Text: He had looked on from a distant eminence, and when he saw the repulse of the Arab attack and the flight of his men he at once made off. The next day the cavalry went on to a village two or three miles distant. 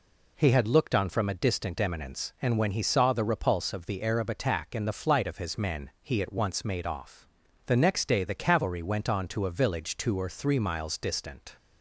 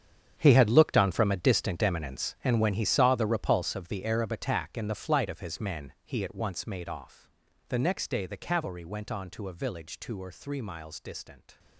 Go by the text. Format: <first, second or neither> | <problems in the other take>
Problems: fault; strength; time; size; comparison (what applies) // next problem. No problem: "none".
first | gets quieter; strong; throughout; 15 dB